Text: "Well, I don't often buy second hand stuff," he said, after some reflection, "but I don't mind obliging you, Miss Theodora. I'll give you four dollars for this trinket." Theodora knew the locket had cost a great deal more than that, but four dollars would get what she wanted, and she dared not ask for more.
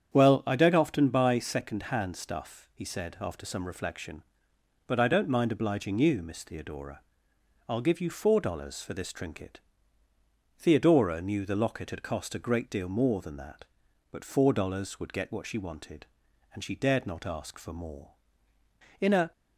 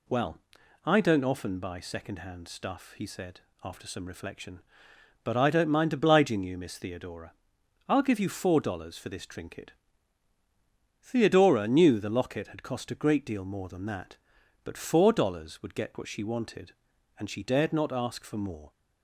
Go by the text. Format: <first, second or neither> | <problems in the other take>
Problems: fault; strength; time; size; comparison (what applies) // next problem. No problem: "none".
second | starts louder than the rest; strong; until 1.1 s; 8.5 dB // goes on to say "In a"; slight; from 18.9 s on; 0.32 s long